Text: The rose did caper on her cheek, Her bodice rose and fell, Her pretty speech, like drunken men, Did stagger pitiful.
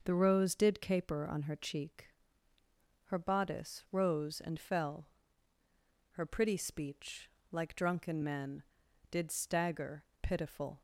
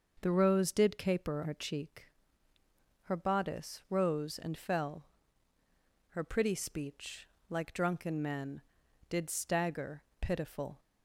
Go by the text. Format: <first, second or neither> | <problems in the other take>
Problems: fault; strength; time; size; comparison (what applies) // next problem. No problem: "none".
first | skips "on"; at 1.4 s // pauses between "stagger" and "pitiful"; slight; at 10.0 s; 0.18 s long; slight in the first